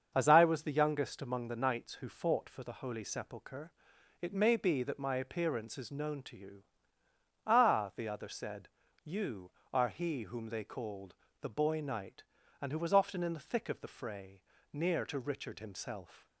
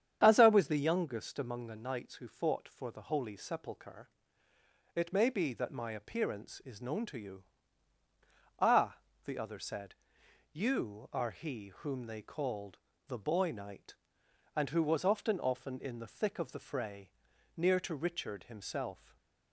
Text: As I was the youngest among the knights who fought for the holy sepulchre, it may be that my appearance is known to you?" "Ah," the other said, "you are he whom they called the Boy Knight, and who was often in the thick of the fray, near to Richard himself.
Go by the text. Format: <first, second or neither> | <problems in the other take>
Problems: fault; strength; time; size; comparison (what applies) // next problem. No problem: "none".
first | starts louder than the rest; strong; until 1.2 s; 9 dB; also in the first // pauses between "called" and "the"; slight; at 12.7 s; 0.30 s long; slight in the first // says "often" twice; at 15.4 s // stays silent after the last word; slight; from 18.9 s on; 0.6 s long